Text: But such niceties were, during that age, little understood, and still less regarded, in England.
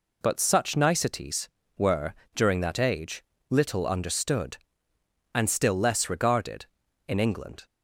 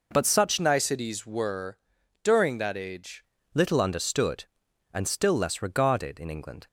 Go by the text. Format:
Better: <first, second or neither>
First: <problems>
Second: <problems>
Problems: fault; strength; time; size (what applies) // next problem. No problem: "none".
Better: first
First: none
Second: changes voice from "niceties" to "age"; from 0.5 to 3.2 s; 2.7 s long